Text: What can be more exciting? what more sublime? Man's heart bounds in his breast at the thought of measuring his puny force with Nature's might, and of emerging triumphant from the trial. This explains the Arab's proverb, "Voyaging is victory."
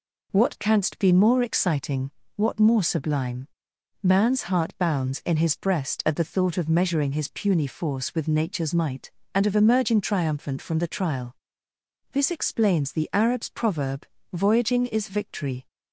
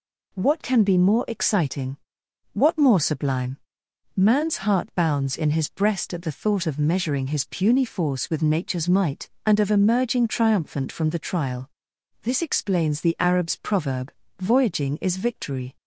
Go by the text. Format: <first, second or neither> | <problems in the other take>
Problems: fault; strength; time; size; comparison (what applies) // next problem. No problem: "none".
second | says "canst" for "can"; at 0.5 s